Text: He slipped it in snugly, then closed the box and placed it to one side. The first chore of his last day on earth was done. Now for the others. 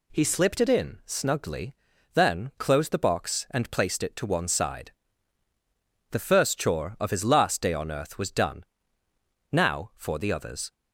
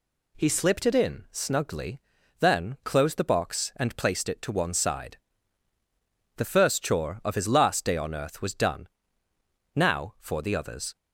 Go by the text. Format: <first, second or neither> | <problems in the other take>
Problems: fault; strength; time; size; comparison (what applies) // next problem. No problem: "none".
neither | none